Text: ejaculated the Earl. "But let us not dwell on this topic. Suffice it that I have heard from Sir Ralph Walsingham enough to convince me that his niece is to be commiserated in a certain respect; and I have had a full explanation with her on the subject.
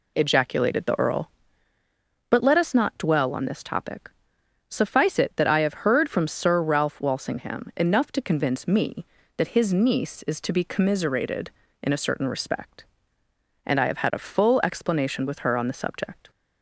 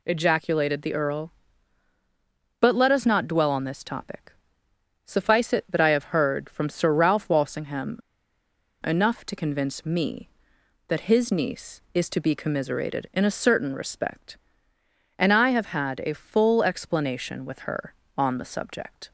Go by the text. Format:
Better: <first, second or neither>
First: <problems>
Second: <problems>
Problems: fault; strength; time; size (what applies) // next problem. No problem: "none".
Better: first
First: none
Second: pauses between "Walsingham" and "enough"; noticeable; at 7.9 s; 0.84 s long